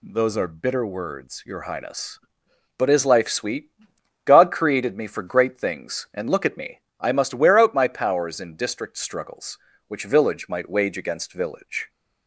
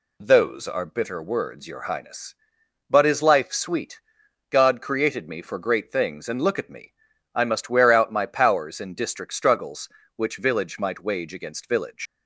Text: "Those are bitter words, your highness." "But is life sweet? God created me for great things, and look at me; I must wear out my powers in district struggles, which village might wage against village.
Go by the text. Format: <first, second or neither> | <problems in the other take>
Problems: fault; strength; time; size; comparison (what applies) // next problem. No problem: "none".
first | leaves "village" unfinished; at 12.0 s; 115 ms